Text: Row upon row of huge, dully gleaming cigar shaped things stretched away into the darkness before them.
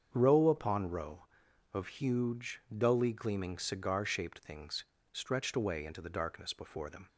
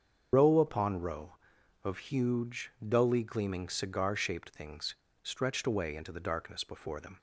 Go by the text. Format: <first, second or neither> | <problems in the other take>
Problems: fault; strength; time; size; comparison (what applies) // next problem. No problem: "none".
first | loses the start of "Row"; at 0.3 s; 90 ms // starts louder than the rest; strong; until 1.3 s; 7 dB; strong in the first // pauses between "things" and "stretched"; slight; at 4.9 s; 0.30 s long; slight in the first